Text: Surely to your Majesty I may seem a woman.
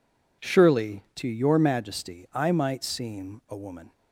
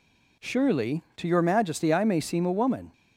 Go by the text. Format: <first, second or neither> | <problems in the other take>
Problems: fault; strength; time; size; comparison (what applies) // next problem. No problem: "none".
second | says "might" for "may"; at 2.5 s